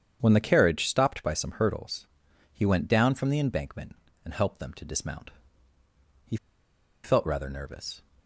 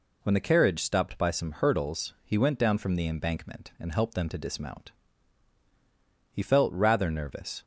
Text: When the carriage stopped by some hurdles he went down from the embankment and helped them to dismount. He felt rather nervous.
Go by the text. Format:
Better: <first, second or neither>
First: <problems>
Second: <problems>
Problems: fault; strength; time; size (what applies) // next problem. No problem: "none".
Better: second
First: starts louder than the rest; strong; until 1.2 s; 8 dB // pauses between "hurdles" and "he"; noticeable; at 2.0 s; 0.48 s long // pauses between "He" and "felt"; noticeable; at 6.3 s; 0.66 s long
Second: none